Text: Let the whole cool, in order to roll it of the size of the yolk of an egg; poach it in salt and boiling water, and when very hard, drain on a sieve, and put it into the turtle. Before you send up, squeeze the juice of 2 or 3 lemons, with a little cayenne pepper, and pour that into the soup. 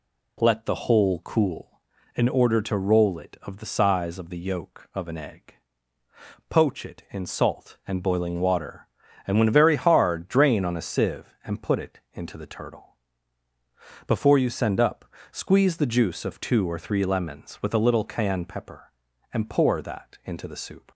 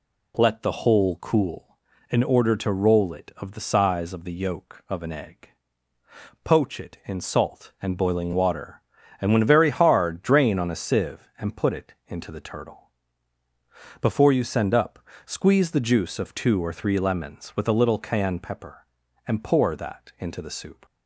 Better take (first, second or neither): neither